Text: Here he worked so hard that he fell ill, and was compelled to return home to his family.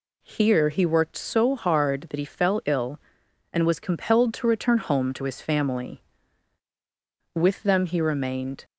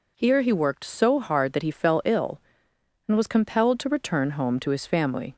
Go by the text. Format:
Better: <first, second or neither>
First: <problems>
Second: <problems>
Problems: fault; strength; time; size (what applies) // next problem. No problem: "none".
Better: second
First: goes on to say "With them he remained"; noticeable; from 7.3 s on; 1.3 s long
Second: none